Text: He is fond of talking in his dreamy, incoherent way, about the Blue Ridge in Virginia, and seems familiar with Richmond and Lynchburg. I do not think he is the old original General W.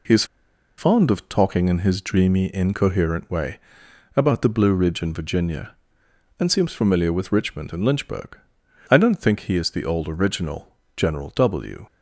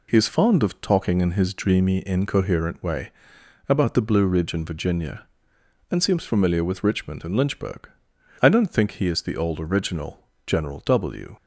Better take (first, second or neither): second